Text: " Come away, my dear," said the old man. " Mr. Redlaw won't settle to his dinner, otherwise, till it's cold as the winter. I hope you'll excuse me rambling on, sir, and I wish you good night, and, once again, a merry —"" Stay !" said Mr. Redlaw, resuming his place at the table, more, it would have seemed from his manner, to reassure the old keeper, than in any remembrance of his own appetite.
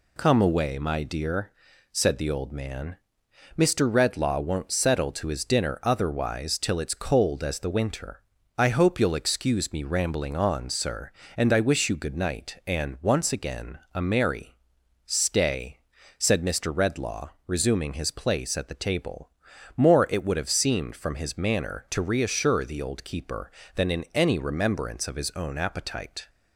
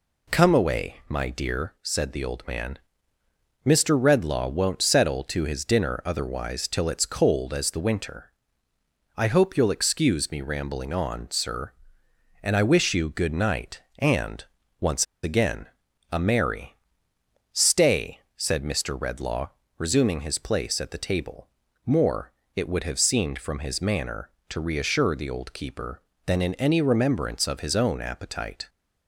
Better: first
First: none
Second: pauses between "once" and "again"; slight; at 15.0 s; 0.19 s long

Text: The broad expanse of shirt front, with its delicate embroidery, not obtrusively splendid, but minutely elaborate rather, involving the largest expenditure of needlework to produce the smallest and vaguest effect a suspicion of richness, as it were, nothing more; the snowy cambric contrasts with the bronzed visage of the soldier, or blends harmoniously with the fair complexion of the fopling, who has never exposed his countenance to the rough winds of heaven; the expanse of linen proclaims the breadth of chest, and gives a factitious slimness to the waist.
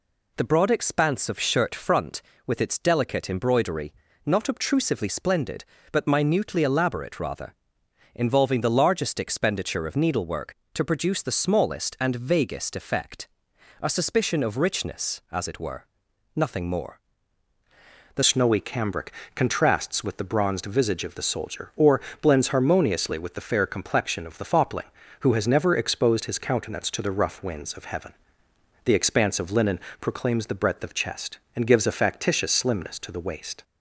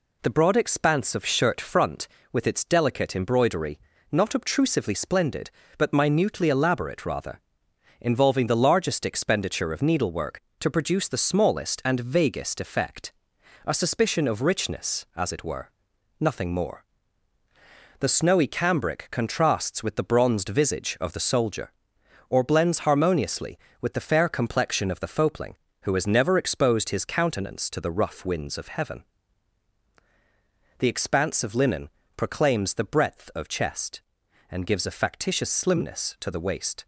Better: second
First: pauses between "effect" and "a"; noticeable; at 13.2 s; 0.58 s long // changes voice at "snowy"; from 18.2 s on; 15.4 s long // pauses between "cambric" and "contrasts"; slight; at 19.1 s; 0.22 s long // pauses between "or" and "blends"; slight; at 22.0 s; 0.22 s long // pauses between "linen" and "proclaims"; slight; at 29.7 s; 0.22 s long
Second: pauses between "effect" and "a"; noticeable; at 13.1 s; 0.58 s long // pauses between "linen" and "proclaims"; slight; at 31.8 s; 0.26 s long

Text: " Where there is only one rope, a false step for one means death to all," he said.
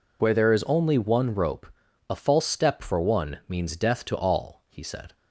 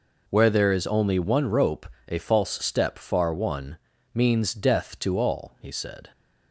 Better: first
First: none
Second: says "far" for "for"; at 2.9 s // pauses between "one" and "means"; slight; at 3.7 s; 0.36 s long

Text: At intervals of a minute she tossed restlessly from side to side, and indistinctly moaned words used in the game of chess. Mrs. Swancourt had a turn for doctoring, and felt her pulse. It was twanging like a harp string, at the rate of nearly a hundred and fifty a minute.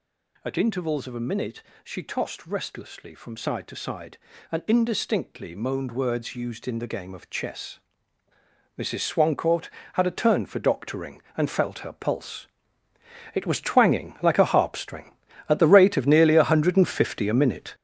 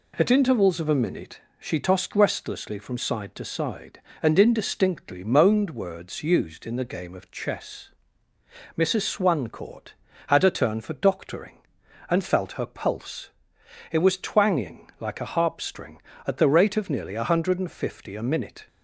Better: second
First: gets louder; strong; throughout; 8.5 dB // pauses between "minute" and "she"; slight; at 1.6 s; 0.20 s long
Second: pauses between "minute" and "she"; slight; at 1.4 s; 0.18 s long

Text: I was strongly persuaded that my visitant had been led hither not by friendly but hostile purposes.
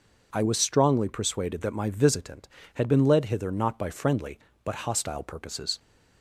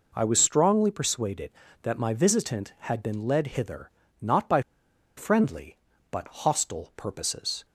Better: first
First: none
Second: pauses between "hither" and "not"; slight; at 3.8 s; 0.32 s long // pauses between "by" and "friendly"; noticeable; at 4.6 s; 0.55 s long

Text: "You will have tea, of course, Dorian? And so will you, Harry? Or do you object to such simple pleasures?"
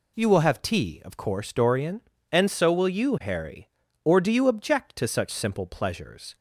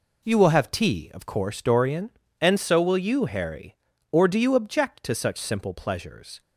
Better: first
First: none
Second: gets quieter; strong; throughout; 9.5 dB

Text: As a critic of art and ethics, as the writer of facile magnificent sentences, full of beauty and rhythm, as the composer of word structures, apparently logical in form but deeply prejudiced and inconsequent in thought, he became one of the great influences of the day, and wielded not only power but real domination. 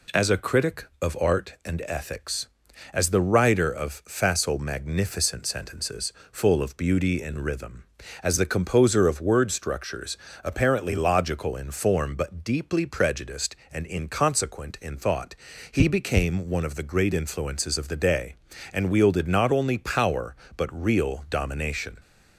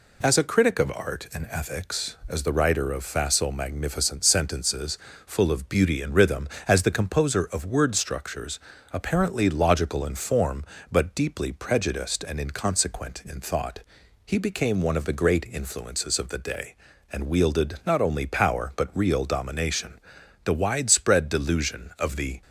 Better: first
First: none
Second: goes on to say "The widespread delusion of the"; strong; from 20.4 s on; 1.9 s long

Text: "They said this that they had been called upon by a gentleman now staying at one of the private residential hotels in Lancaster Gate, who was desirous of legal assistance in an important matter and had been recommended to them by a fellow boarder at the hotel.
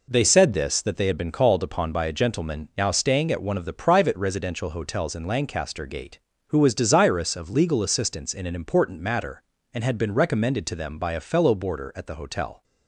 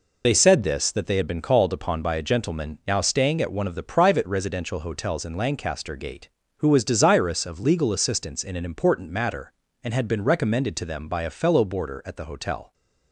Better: first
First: none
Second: loses the start of "They"; at 0.2 s; 70 ms

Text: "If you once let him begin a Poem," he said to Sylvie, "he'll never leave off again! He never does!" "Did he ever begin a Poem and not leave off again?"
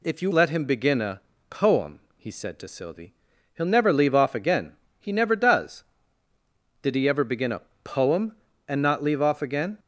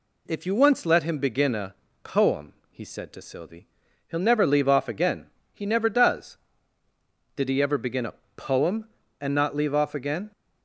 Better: second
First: skips "once"; at 0.3 s // pauses between "a" and "Poem"; slight; at 1.2 s; 0.28 s long // pauses between "a" and "Poem"; slight; at 7.6 s; 0.20 s long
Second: pauses between "a" and "Poem"; slight; at 1.7 s; 0.28 s long // pauses between "a" and "Poem"; slight; at 8.1 s; 0.20 s long

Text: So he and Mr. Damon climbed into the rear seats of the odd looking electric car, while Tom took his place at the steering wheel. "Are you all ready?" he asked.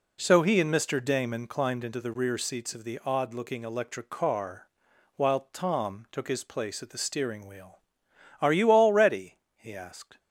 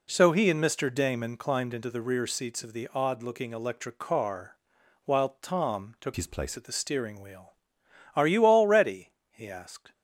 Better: first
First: none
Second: changes voice from "his" to "place"; from 6.1 to 6.5 s; 0.4 s long

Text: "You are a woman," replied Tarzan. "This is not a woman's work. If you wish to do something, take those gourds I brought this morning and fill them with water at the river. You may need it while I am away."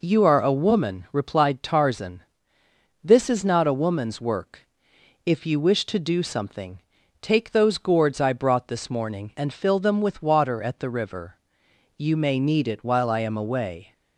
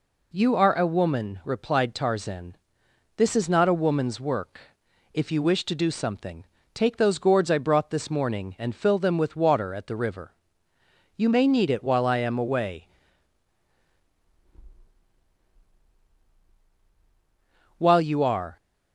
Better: first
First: none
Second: goes on to say "While you are"; noticeable; from 17.7 s on; 0.80 s long

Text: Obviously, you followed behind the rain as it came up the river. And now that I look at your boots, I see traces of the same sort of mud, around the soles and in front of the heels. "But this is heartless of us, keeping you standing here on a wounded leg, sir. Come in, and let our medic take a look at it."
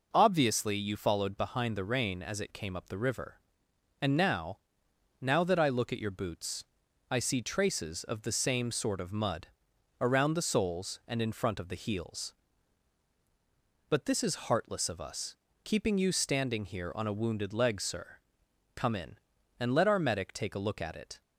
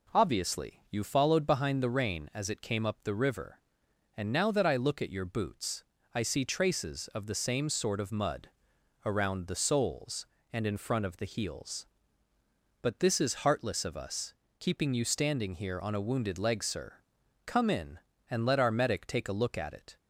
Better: second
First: says "now" twice; at 5.2 s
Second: none

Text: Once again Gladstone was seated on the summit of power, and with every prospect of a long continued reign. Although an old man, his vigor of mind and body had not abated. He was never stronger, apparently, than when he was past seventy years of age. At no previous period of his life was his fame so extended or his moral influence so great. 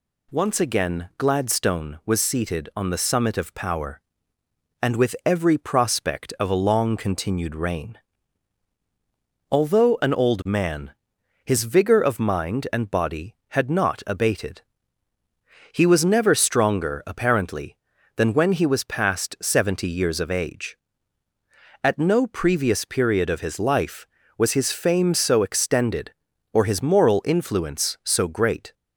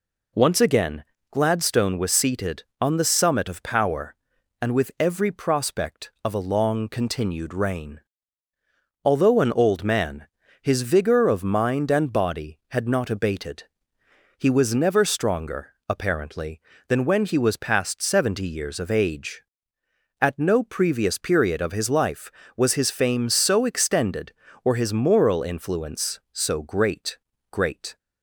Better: first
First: none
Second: pauses between "again" and "Gladstone"; slight; at 1.0 s; 0.26 s long // says "great" twice; at 27.5 s

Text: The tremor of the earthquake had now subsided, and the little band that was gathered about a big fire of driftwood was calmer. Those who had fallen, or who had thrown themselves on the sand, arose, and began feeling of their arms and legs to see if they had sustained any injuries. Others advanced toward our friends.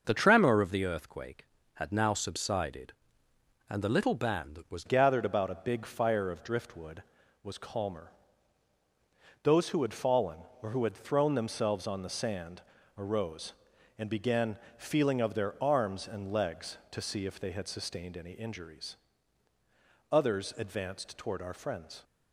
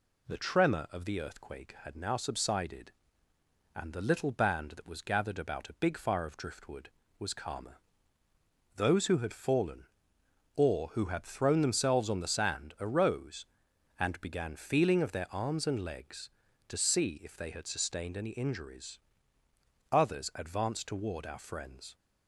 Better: second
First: starts louder than the rest; until 1.0 s; 6.5 dB // changes voice at "gathered"; from 4.8 s on; 17.2 s long // pauses between "began" and "feeling"; slight; at 14.5 s; 0.20 s long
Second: none

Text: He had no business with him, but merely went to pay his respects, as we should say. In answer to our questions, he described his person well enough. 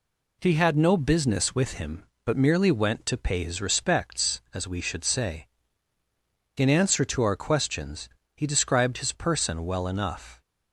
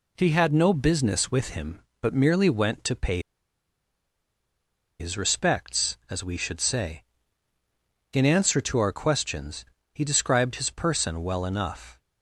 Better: first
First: none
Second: pauses between "pay" and "his"; strong; at 3.2 s; 1.7 s long

